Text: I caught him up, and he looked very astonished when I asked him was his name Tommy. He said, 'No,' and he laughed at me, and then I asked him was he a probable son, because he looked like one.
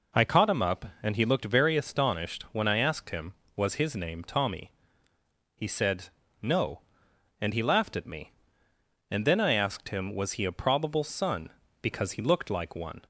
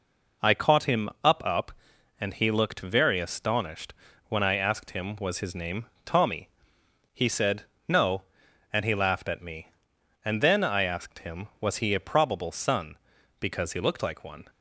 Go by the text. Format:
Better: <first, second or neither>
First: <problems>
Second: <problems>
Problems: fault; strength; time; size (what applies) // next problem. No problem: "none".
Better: first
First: none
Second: says "up" twice; at 1.4 s // pauses between "astonished" and "when"; slight; at 3.9 s; 0.34 s long // pauses between "name" and "Tommy"; slight; at 5.8 s; 0.18 s long